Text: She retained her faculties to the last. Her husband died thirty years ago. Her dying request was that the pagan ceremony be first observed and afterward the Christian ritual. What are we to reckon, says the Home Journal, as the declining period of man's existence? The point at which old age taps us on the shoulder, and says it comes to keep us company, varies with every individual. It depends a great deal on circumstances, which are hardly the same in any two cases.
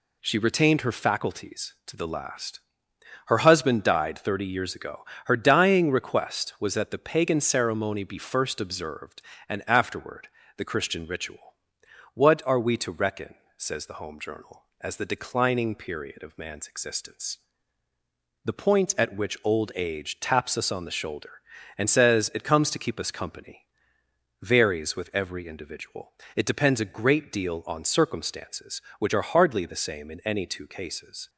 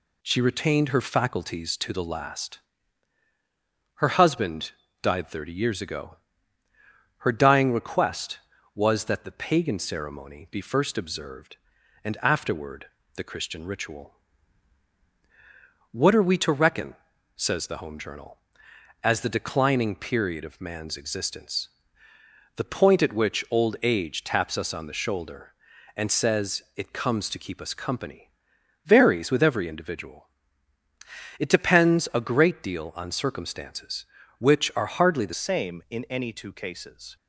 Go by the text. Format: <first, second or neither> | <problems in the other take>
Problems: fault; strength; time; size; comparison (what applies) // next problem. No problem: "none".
first | pauses between "husband" and "died"; slight; at 4.7 s; 0.32 s long // pauses between "afterward" and "the"; slight; at 12.8 s; 0.28 s long; slight in the first // changes voice at "same"; from 35.3 s on; 1.8 s long